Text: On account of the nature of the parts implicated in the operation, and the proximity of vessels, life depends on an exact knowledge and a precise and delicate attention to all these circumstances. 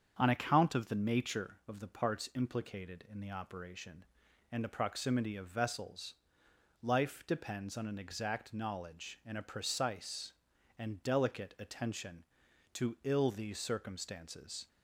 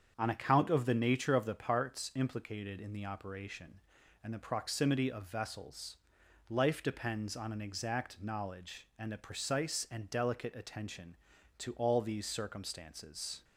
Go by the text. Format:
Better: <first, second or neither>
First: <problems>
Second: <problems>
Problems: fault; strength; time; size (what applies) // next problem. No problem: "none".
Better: second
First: starts louder than the rest; strong; until 1.2 s; 7.5 dB // says "ill" for "all"; at 13.0 s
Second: starts louder than the rest; strong; until 1.1 s; 7.5 dB